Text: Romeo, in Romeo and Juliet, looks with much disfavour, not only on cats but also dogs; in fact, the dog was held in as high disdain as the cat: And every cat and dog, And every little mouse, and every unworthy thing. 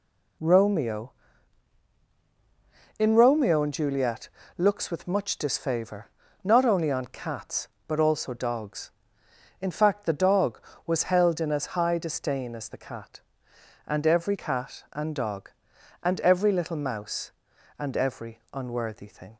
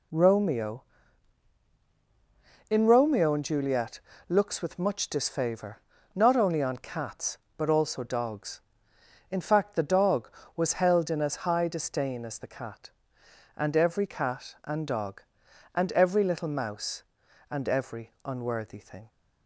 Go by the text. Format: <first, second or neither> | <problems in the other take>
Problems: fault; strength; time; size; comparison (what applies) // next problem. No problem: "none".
neither | none